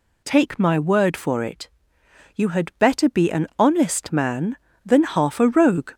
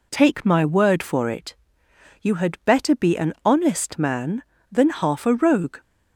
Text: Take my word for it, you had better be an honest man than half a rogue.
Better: second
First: gets louder; slight; throughout; 2.5 dB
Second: none

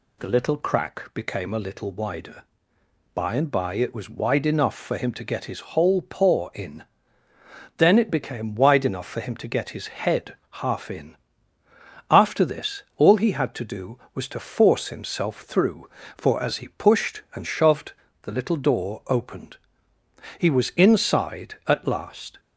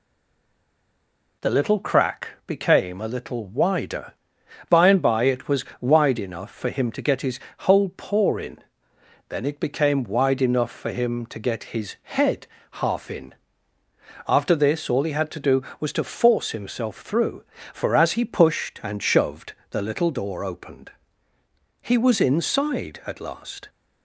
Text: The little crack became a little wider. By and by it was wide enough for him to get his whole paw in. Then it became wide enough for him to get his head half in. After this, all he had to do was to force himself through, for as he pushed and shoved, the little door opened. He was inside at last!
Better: first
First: pauses between "head" and "half"; slight; at 10.3 s; 0.16 s long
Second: stays silent before the first word; noticeable; until 1.4 s; 1.4 s long // pauses between "crack" and "became"; slight; at 2.3 s; 0.16 s long // pauses between "was" and "wide"; slight; at 5.6 s; 0.16 s long // pauses between "his" and "whole"; slight; at 7.3 s; 0.20 s long // pauses between "head" and "half"; slight; at 12.4 s; 0.24 s long

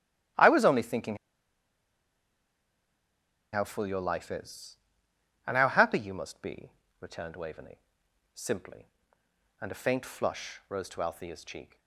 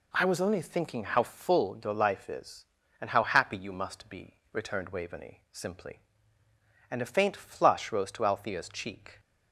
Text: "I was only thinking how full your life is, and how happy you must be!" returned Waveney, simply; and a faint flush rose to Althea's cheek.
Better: second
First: starts louder than the rest; strong; until 3.7 s; 13 dB // pauses between "thinking" and "how"; strong; at 1.1 s; 2.3 s long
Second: none

